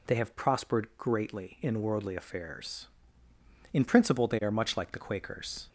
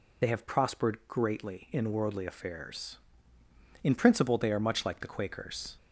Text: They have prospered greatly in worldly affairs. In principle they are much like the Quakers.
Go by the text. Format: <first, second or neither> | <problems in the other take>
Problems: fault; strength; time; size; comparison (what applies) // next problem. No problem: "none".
first | loses the start of "They"; at 0.2 s; 25 ms